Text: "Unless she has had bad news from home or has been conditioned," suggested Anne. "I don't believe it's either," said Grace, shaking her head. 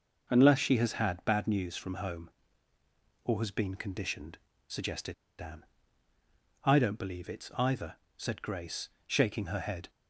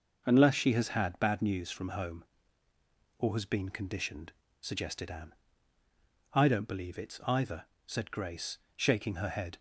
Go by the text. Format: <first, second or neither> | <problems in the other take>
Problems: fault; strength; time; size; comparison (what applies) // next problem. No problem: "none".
second | pauses between "suggested" and "Anne"; slight; at 5.1 s; 0.26 s long